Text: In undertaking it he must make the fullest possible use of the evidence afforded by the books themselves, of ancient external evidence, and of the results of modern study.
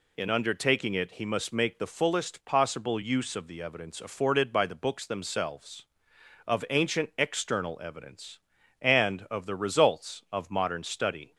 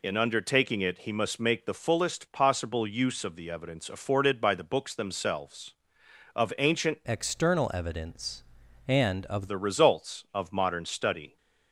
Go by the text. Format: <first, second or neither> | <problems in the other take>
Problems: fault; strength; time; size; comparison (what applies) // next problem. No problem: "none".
first | changes voice from "external" to "of"; from 7.0 to 9.4 s; 2.4 s long